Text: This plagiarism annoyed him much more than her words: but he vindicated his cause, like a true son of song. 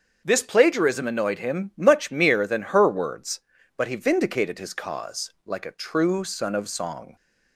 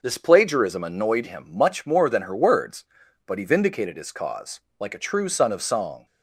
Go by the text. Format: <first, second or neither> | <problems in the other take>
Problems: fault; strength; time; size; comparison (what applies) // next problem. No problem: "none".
second | starts louder than the rest; until 1.2 s; 7 dB // says "mere" for "more"; at 2.1 s